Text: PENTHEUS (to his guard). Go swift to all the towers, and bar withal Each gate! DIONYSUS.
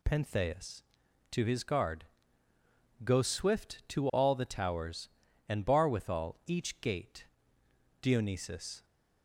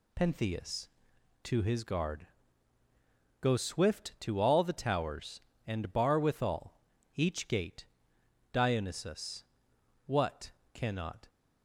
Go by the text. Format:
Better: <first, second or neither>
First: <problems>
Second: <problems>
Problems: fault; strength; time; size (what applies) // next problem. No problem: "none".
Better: first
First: none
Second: pauses between "withal" and "Each"; slight; at 6.8 s; 0.34 s long // goes on to say "What cannot"; noticeable; from 10.0 s on; 1.2 s long